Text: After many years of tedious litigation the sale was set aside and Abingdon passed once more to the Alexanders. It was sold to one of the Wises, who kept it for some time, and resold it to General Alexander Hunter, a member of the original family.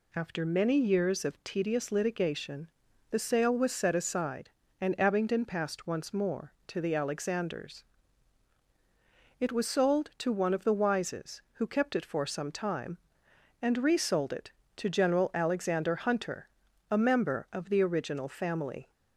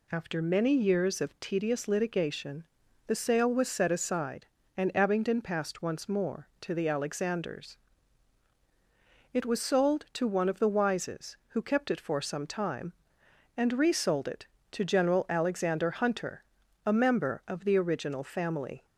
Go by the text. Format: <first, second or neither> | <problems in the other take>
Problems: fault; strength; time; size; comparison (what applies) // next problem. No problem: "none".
neither | pauses between "litigation" and "the"; the same in both